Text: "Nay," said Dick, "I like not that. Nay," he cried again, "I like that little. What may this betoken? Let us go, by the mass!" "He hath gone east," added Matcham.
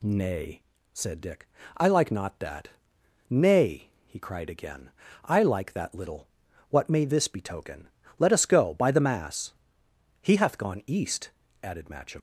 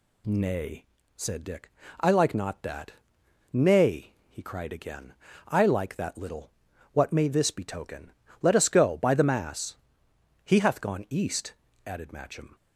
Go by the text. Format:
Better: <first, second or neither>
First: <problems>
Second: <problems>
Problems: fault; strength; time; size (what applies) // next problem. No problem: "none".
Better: second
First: leaves "Matcham" unfinished; at 12.1 s; 115 ms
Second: none